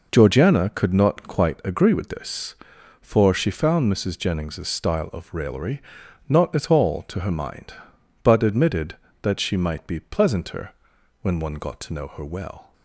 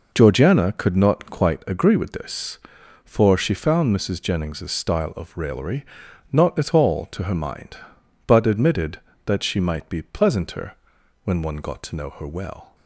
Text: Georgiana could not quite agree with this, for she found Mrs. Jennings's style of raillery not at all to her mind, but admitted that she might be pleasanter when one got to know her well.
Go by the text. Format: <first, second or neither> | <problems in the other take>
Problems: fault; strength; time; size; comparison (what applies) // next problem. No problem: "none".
neither | pauses between "raillery" and "not"; noticeable; the same in both // pauses between "pleasanter" and "when"; noticeable; the same in both